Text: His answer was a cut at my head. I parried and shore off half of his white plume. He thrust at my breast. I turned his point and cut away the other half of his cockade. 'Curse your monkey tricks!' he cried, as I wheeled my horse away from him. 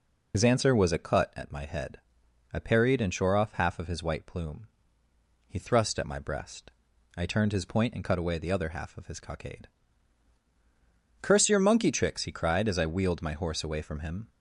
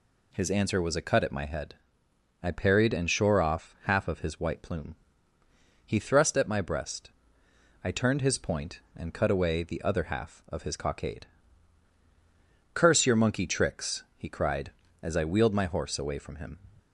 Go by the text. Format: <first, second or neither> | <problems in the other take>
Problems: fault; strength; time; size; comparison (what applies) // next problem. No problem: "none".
second | loses the start of "His"; at 0.3 s; 60 ms